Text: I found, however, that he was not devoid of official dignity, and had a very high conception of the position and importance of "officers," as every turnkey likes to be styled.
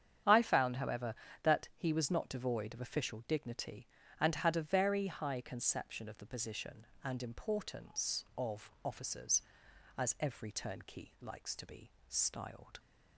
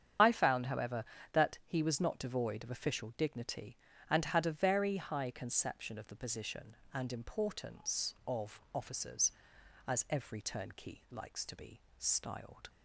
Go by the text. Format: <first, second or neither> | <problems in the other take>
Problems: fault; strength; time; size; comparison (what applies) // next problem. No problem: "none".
first | loses the start of "I"; at 0.1 s; 45 ms // starts louder than the rest; strong; until 1.4 s; 8.5 dB; strong in the first // pauses between "be" and "styled"; slight; at 11.7 s; 0.18 s long; slight in the first